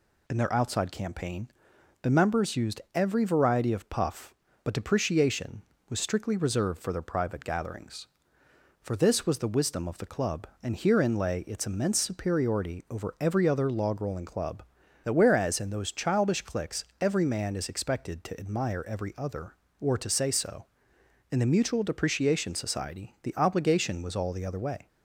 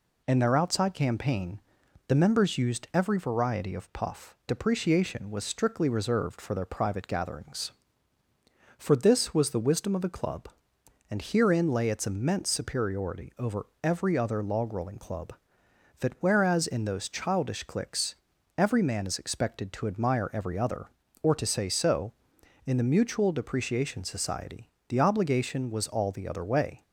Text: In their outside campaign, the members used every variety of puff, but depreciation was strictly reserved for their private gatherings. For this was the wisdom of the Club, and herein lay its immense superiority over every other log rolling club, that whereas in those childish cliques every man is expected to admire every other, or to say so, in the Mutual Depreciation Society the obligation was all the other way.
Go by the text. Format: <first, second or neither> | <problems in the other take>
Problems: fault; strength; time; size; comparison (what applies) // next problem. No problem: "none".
first | skips "but"; at 4.4 s // pauses between "over" and "every"; slight; at 13.6 s; 0.18 s long // pauses between "cliques" and "every"; at 18.1 s; 0.42 s long; slight in the first // pauses between "Society" and "the"; slight; at 24.6 s; 0.20 s long